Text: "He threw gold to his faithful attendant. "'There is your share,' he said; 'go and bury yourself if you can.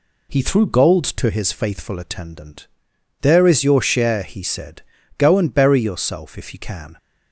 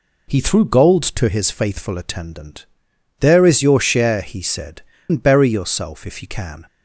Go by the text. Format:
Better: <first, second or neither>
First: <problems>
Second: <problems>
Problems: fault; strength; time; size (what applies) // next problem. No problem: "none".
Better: first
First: none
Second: skips "go"; at 4.9 s